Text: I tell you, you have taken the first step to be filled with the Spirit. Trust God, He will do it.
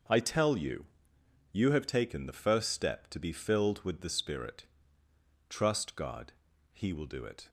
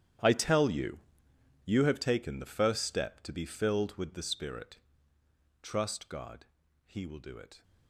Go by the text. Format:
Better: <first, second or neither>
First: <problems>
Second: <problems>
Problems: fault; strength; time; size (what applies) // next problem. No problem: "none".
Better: first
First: starts louder than the rest; until 1.7 s; 6.5 dB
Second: gets quieter; strong; throughout; 17 dB // starts louder than the rest; strong; until 1.8 s; 10.5 dB